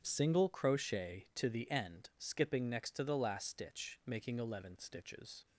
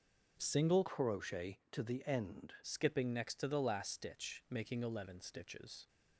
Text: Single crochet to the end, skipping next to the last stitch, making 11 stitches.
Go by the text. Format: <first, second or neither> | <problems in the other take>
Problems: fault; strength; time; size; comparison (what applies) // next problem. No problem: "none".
first | starts louder than the rest; until 1.4 s; 7 dB; strong in the first // changes voice from "crochet" to "end"; from 0.8 to 2.5 s; 1.7 s long